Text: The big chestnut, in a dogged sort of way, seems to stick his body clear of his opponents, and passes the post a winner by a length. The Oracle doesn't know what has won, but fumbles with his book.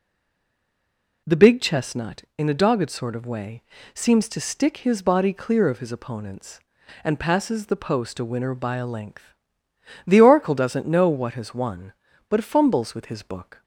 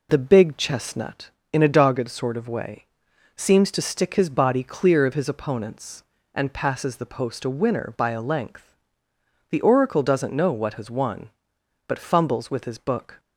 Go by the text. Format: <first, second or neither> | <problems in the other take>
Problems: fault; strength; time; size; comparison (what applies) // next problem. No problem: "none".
second | stays silent before the first word; noticeable; until 1.2 s; 1.2 s long